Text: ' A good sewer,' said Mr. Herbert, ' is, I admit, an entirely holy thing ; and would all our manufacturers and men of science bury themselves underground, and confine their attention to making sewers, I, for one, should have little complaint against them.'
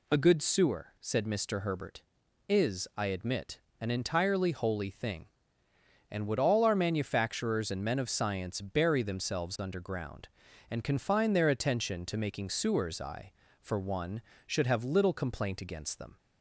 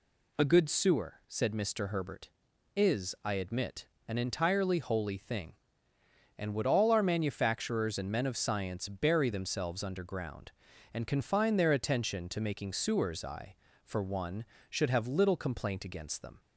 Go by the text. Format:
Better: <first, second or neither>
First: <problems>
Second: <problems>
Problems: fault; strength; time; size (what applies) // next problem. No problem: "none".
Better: neither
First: none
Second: none